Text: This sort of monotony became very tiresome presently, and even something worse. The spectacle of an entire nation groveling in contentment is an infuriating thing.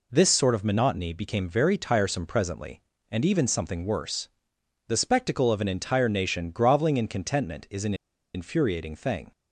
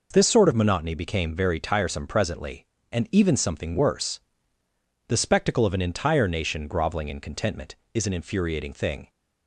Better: second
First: pauses between "an" and "infuriating"; at 7.9 s; 0.41 s long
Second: none

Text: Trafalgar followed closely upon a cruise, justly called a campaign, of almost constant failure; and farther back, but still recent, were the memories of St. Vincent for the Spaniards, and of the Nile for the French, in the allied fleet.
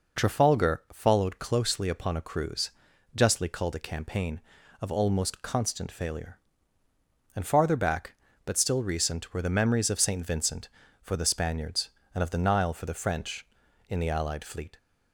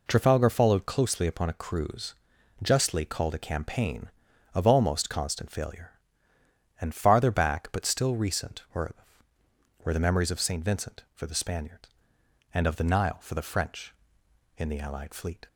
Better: first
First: none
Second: says "were" twice; at 9.8 s

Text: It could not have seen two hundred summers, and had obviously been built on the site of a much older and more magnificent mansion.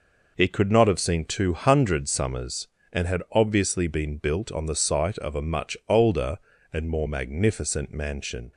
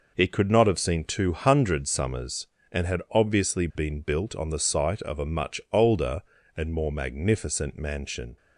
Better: neither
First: none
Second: none

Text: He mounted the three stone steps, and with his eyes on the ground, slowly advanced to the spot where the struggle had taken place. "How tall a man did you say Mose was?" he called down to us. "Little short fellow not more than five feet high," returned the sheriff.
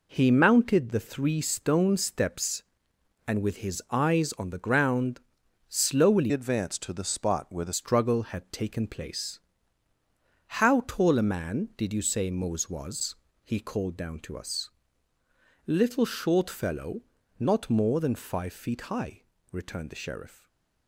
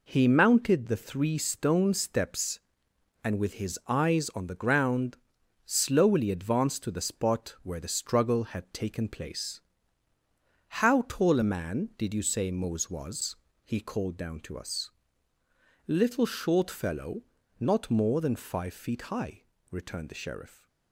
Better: second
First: changes voice from "advanced" to "the"; from 6.3 to 7.7 s; 1.4 s long // pauses between "fellow" and "not"; slight; at 17.0 s; 0.36 s long // stays silent after the last word; slight; from 20.3 s on; 0.5 s long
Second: pauses between "fellow" and "not"; slight; at 17.2 s; 0.36 s long

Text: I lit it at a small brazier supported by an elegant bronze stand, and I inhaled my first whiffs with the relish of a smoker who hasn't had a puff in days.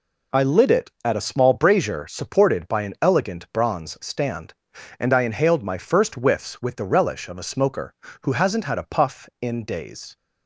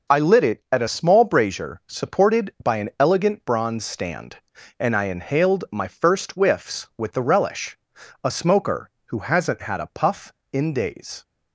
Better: first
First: none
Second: skips "of"; at 7.9 s

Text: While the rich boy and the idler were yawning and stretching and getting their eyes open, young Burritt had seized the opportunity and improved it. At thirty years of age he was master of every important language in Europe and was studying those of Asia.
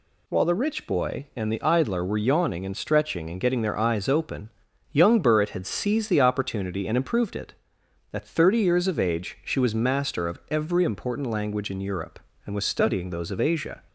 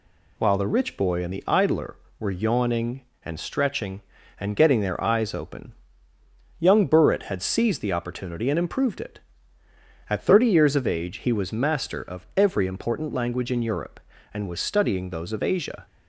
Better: second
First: says "she" for "he"; at 9.4 s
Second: none

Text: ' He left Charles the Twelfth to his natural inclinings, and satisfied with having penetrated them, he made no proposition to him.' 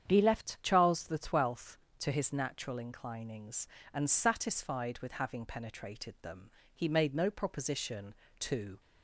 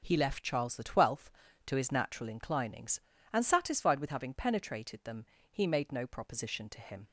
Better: second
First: starts louder than the rest; strong; until 1.1 s; 8.5 dB // stops before "him"; at 8.7 s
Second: starts louder than the rest; until 1.0 s; 6 dB

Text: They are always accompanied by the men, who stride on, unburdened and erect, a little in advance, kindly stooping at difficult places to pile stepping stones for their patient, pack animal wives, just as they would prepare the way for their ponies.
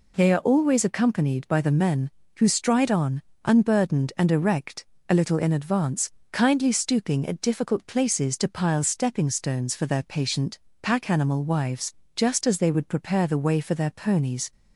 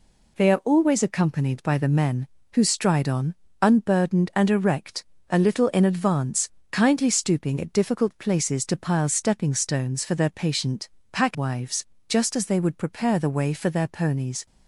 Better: first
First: none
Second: skips "animal"; at 11.3 s

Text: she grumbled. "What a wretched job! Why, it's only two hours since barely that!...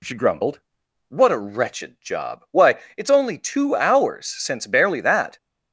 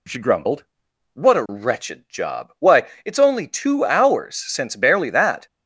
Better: neither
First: none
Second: none

